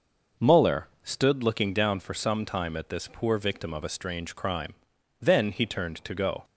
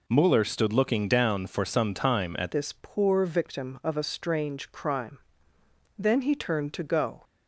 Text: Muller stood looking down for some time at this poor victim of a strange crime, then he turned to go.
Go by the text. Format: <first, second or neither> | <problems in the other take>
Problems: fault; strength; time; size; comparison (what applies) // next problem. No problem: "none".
first | changes voice at "this"; from 2.5 s on; 4.7 s long